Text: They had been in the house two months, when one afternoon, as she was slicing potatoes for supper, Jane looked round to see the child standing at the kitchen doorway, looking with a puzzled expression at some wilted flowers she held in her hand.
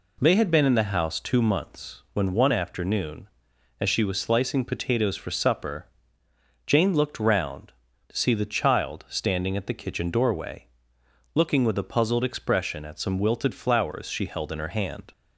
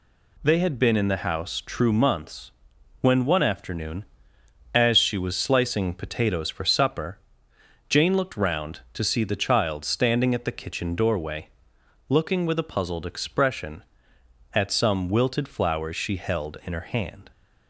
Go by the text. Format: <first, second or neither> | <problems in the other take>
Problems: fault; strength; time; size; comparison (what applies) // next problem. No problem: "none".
first | says "true" for "two"; at 1.6 s